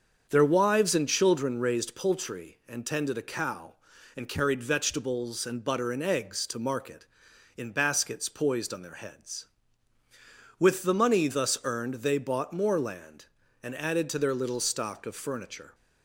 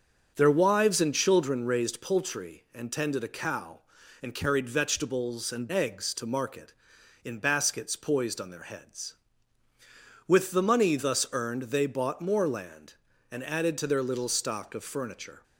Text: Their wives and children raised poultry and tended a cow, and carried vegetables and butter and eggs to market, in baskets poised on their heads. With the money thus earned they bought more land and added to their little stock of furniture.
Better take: first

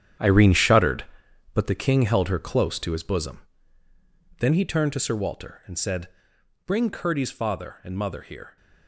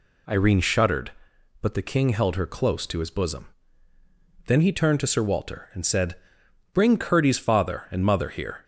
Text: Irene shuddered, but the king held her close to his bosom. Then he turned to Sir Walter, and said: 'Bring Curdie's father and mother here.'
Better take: second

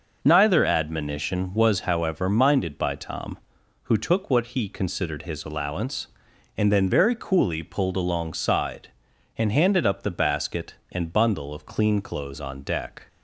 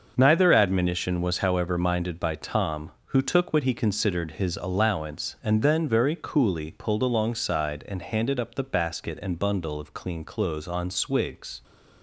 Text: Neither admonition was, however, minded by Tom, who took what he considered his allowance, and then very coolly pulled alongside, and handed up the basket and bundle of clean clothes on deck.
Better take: first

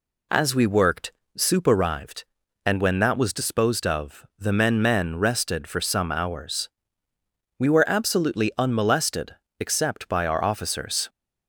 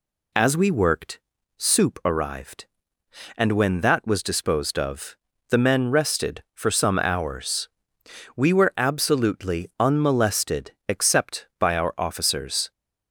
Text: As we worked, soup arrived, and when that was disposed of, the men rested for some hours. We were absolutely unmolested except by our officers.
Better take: second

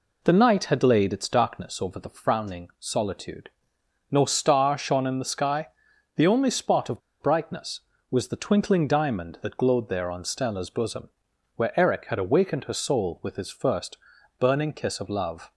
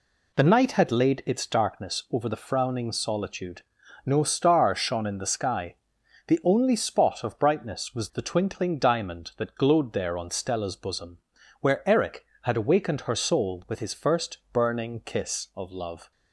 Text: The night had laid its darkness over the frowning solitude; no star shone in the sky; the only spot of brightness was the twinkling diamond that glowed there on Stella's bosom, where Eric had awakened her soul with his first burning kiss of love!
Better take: second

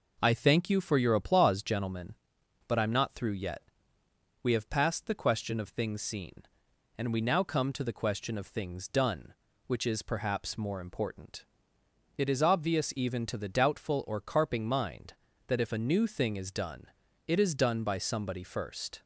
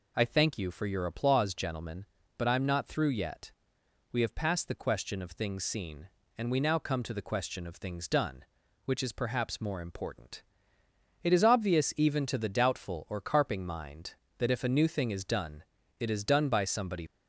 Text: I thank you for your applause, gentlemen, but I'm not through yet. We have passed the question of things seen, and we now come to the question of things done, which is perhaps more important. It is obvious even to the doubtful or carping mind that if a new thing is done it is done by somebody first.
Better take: first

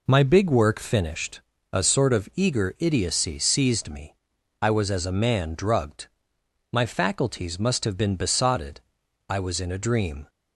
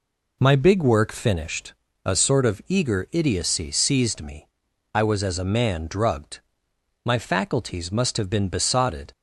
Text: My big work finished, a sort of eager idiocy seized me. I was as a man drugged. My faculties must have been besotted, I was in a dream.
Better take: first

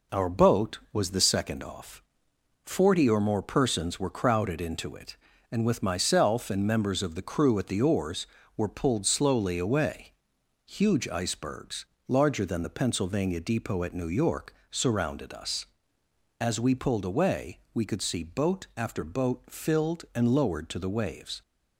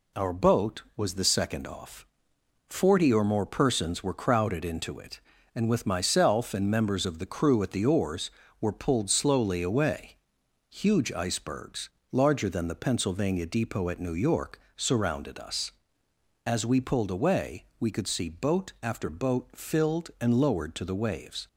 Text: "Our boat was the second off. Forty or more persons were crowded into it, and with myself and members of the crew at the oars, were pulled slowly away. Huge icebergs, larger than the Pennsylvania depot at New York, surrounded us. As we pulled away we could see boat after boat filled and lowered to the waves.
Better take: second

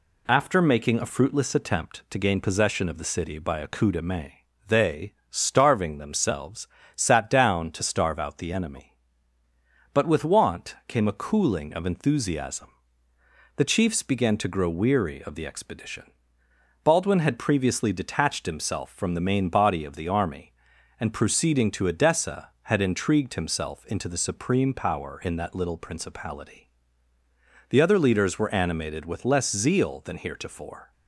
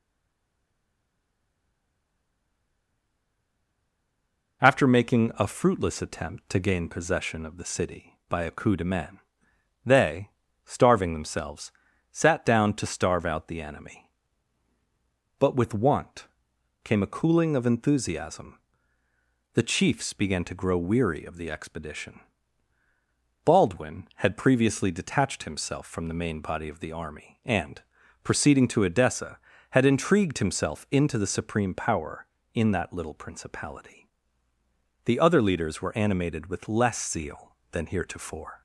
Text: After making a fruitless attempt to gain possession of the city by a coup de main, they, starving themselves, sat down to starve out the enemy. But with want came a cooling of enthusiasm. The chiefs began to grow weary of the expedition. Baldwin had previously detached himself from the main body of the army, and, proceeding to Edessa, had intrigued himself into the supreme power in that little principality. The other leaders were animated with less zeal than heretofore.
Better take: first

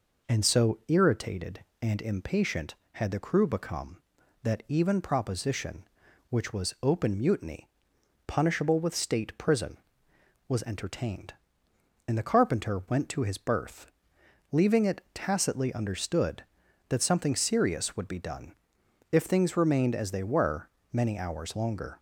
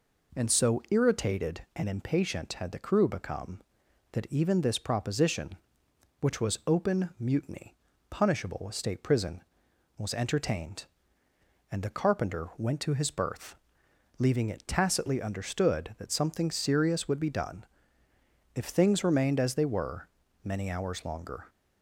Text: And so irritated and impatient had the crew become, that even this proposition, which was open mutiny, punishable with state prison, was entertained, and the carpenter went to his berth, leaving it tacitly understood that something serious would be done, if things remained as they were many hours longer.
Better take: second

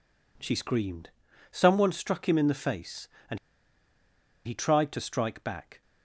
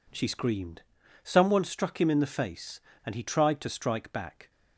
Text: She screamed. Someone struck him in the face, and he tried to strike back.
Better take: second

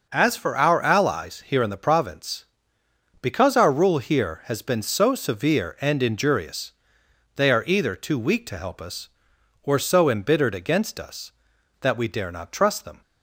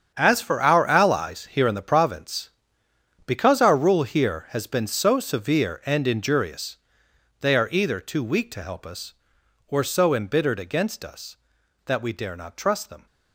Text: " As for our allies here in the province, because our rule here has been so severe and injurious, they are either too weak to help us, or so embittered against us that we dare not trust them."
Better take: first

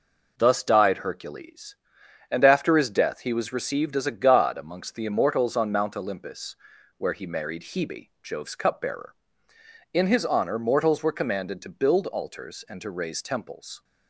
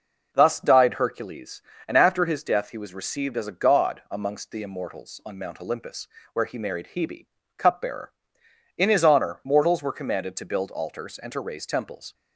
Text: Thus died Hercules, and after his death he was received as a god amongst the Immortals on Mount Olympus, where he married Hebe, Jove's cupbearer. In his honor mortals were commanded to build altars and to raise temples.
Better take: first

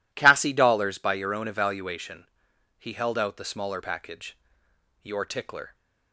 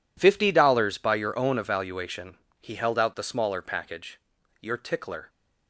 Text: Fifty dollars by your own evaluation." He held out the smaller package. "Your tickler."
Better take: second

